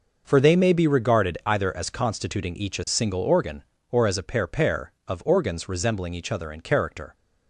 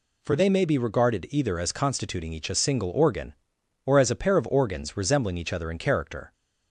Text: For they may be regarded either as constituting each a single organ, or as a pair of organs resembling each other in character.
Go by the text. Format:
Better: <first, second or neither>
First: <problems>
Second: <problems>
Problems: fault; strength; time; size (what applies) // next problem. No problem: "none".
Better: second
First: says "pair" twice; at 4.4 s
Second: none